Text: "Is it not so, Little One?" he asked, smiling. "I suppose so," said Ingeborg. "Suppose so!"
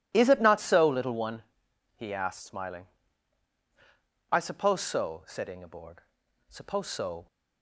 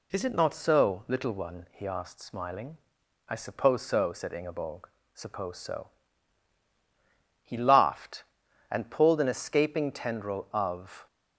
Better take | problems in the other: first | goes on to say "He laughed and pulled an escaping tendril of"; strong; from 7.4 s on; 3.6 s long

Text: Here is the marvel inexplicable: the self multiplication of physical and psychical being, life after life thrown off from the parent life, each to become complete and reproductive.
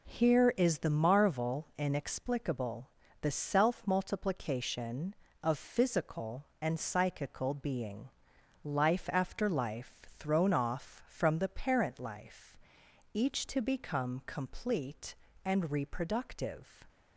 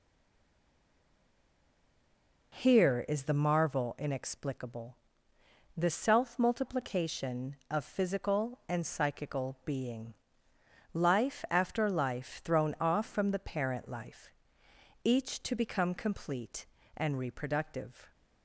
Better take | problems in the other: first | stays silent before the first word; until 2.5 s; 2.5 s long

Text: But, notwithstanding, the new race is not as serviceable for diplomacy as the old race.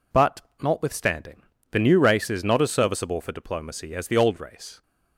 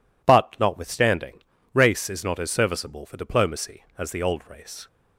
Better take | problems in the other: first | skips "the new"; at 1.5 s

